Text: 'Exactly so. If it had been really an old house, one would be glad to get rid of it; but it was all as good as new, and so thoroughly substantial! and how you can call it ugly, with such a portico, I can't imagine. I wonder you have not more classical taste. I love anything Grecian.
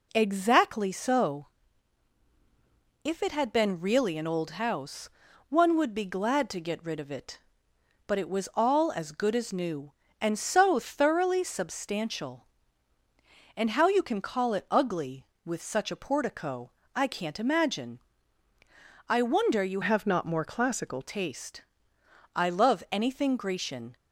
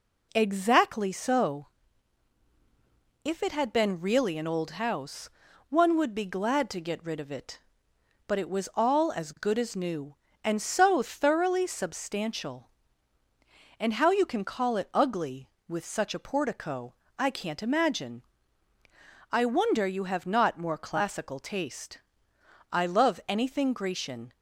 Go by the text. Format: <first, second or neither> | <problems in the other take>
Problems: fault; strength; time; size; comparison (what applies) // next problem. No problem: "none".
second | changes voice from "have" to "classical"; from 19.8 to 21.0 s; 1.2 s long